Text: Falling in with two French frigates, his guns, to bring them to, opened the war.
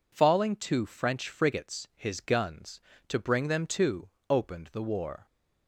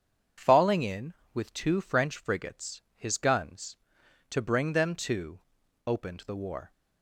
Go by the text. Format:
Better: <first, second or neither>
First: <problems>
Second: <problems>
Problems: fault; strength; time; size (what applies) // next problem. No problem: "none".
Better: second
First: skips "in with"; at 0.5 s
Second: none